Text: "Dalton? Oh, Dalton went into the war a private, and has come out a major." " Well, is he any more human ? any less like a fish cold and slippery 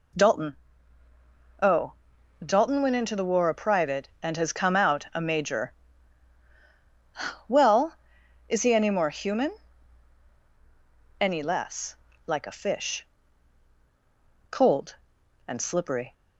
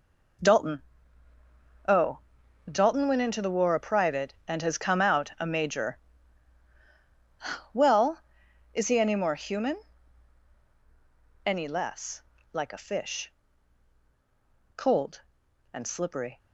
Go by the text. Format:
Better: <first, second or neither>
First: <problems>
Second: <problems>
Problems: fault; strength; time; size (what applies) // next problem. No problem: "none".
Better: first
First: pauses between "less" and "like"; slight; at 11.9 s; 0.32 s long // pauses between "fish" and "cold"; strong; at 13.0 s; 1.4 s long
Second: gets quieter; strong; throughout; 8.5 dB // pauses between "less" and "like"; slight; at 12.2 s; 0.32 s long // pauses between "fish" and "cold"; strong; at 13.3 s; 1.4 s long